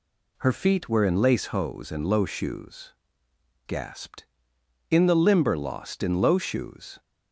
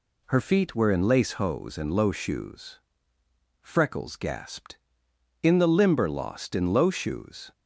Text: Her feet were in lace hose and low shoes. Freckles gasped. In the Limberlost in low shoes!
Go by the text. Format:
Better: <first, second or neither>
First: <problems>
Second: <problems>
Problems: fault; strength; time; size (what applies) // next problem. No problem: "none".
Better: second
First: skips "Freckles"; at 3.2 s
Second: none